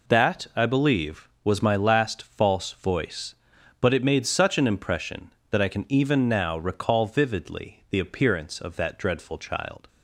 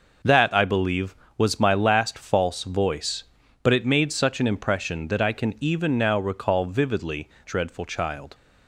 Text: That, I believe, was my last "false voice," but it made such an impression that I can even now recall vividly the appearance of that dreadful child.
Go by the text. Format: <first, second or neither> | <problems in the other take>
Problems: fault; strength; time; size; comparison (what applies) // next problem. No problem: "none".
first | skips "the appearance of that"; at 7.3 s